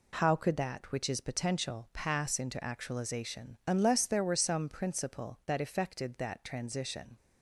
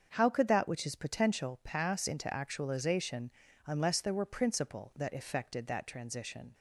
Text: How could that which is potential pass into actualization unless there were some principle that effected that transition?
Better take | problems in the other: first | starts louder than the rest; until 1.1 s; 7 dB // pauses between "actualization" and "unless"; slight; at 3.2 s; 0.36 s long // skips "some"; at 4.2 s

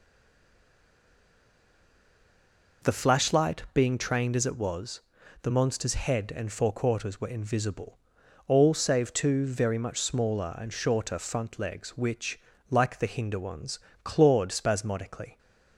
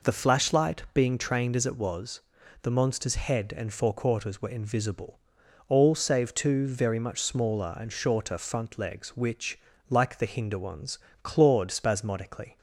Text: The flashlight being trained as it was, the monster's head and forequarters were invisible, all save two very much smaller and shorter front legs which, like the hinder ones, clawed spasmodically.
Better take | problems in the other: second | stays silent before the first word; strong; until 2.8 s; 2.8 s long

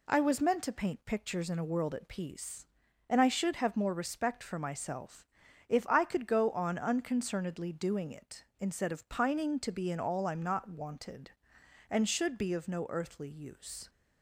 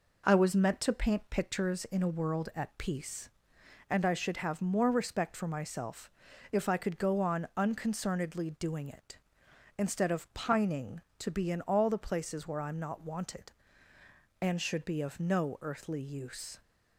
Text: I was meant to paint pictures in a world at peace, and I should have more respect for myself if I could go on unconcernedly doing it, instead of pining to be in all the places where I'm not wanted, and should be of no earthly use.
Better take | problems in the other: second | pauses between "myself" and "if"; at 5.2 s; 0.44 s long; also in the second // skips "the places where"; at 10.2 s

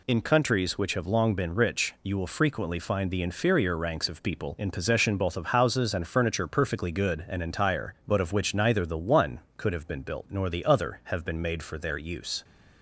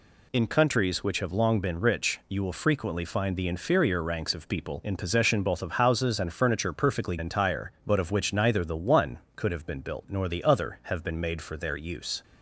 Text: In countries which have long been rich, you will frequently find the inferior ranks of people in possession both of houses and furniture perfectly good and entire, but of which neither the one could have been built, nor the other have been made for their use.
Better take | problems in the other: first | skips "good and"; at 7.1 s

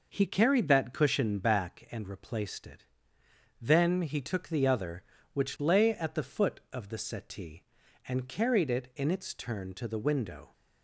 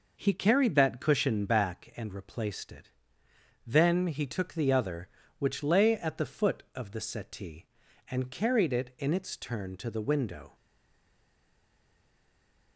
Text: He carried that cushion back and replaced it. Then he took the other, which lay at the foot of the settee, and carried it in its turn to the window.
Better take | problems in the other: first | stays silent after the last word; from 10.5 s on; 2.2 s long

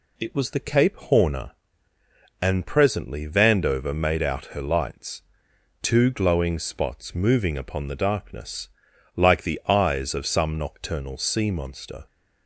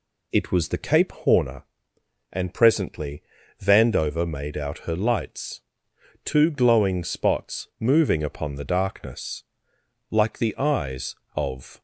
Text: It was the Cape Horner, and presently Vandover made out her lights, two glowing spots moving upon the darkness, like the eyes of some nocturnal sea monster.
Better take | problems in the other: first | pauses between "presently" and "Vandover"; at 3.2 s; 0.38 s long // stops before "some nocturnal sea monster"; at 11.7 s

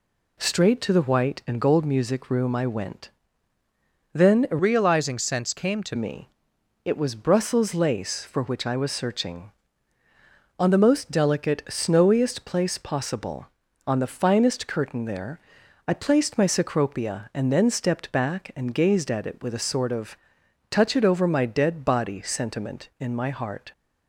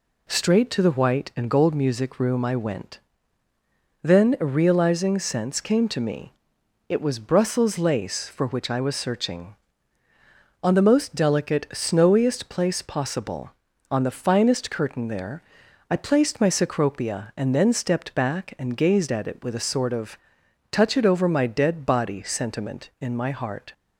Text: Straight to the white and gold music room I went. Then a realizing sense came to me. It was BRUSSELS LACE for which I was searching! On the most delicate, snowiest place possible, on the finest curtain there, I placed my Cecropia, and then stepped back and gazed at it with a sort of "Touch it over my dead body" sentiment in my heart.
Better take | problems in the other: second | changes voice from "realizing" to "to"; from 4.5 to 5.9 s; 1.4 s long // pauses between "of" and "Touch"; noticeable; at 20.1 s; 0.54 s long; noticeable in the second

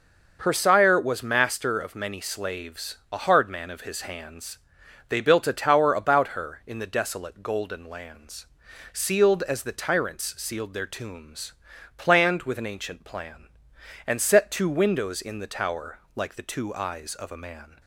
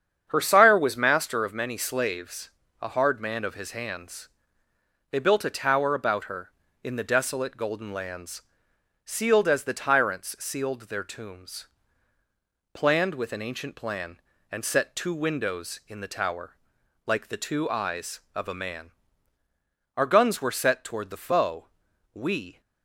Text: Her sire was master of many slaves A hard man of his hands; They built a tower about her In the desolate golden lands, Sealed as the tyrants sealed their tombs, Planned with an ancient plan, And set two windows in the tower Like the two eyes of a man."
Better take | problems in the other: first | starts louder than the rest; strong; until 1.3 s; 8 dB // pauses between "slaves" and "A"; slight; at 2.5 s; 0.30 s long; slight in the first // pauses between "tower" and "Like"; noticeable; at 16.5 s; 0.50 s long; slight in the first // goes on to say "Our guns were set toward the foe we"; strong; from 19.9 s on; 2.6 s long

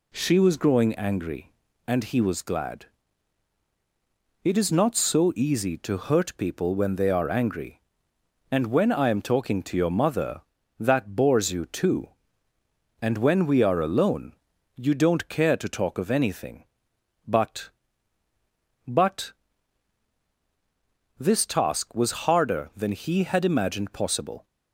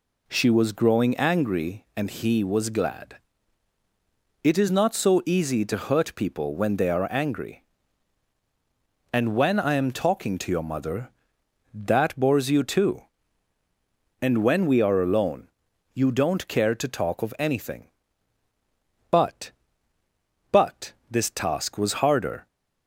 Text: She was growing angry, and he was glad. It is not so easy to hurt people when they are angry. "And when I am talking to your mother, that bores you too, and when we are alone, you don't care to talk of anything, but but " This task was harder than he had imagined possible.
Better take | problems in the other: first | stops before "than he had imagined possible"; at 22.4 s

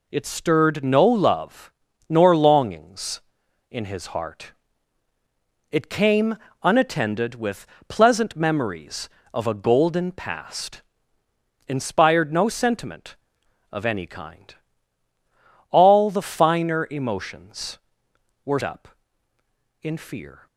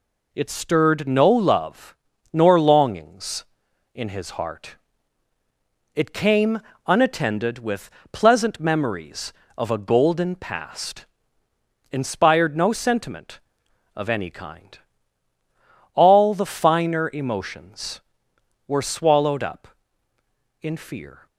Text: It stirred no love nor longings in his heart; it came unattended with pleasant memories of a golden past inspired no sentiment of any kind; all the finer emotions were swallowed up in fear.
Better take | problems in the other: second | pauses between "love" and "nor"; slight; at 1.7 s; 0.36 s long; slight in the second // pauses between "came" and "unattended"; slight; at 6.3 s; 0.26 s long; slight in the second // pauses between "with" and "pleasant"; slight; at 7.6 s; 0.24 s long; slight in the second // pauses between "past" and "inspired"; noticeable; at 10.7 s; 0.88 s long; noticeable in the second // skips "swallowed"; at 18.6 s

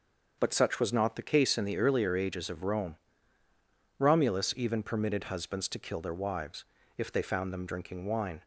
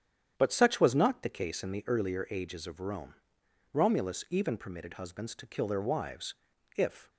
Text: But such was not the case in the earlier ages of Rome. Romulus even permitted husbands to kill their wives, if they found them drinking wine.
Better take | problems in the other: first | starts louder than the rest; strong; until 1.3 s; 9 dB; also in the first // stops before "they found them drinking wine"; at 7.0 s

